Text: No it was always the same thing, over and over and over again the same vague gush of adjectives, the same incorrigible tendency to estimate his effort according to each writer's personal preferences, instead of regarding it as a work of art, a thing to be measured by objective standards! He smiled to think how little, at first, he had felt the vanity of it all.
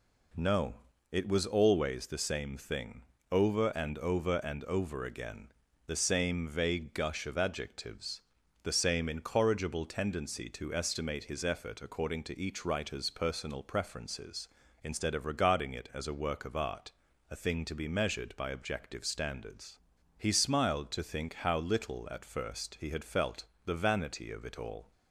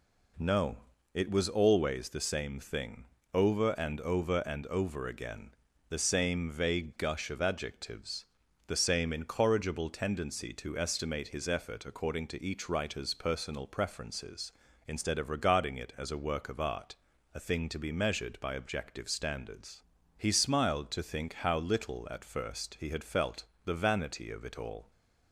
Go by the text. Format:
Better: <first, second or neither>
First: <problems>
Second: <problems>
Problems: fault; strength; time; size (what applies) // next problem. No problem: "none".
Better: neither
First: pauses between "No" and "it"; slight; at 0.7 s; 0.34 s long // pauses between "again" and "the"; slight; at 5.5 s; 0.36 s long // pauses between "felt" and "the"; slight; at 23.4 s; 0.18 s long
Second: pauses between "No" and "it"; slight; at 0.7 s; 0.34 s long // pauses between "again" and "the"; slight; at 5.5 s; 0.36 s long // pauses between "felt" and "the"; slight; at 23.4 s; 0.18 s long